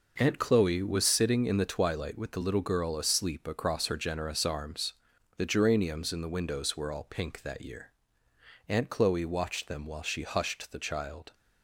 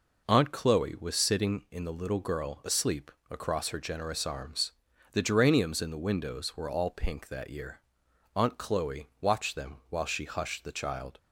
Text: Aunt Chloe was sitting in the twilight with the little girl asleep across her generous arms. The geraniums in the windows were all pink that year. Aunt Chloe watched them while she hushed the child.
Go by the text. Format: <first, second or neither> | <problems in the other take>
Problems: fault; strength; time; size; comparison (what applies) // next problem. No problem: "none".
first | skips "twilight with the"; at 1.9 s // pauses between "asleep" and "across"; slight; at 3.1 s; 0.18 s long